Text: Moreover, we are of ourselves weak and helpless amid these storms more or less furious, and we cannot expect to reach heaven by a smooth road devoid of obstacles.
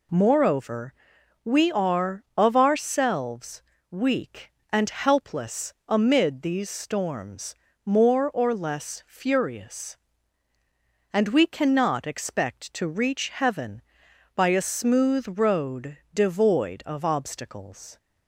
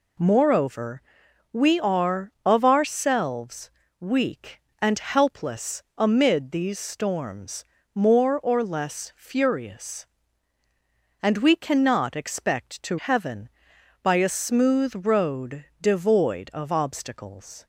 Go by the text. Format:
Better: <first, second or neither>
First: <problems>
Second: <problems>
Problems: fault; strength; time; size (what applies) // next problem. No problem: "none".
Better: first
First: pauses between "ourselves" and "weak"; slight; at 3.6 s; 0.28 s long // pauses between "storms" and "more"; slight; at 7.5 s; 0.30 s long // pauses between "road" and "devoid"; slight; at 15.9 s; 0.16 s long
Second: pauses between "ourselves" and "weak"; slight; at 3.7 s; 0.30 s long // pauses between "storms" and "more"; slight; at 7.6 s; 0.30 s long // skips "reach"; at 12.9 s // pauses between "road" and "devoid"; slight; at 15.6 s; 0.16 s long